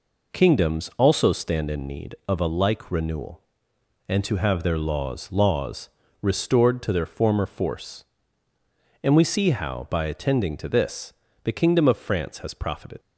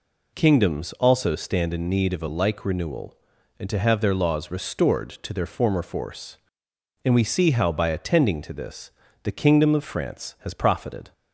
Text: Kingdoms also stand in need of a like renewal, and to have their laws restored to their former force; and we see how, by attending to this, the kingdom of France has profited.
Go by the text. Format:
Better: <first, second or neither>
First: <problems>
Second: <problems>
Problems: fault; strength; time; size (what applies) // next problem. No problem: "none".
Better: second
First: says "laws" twice; at 5.3 s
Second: none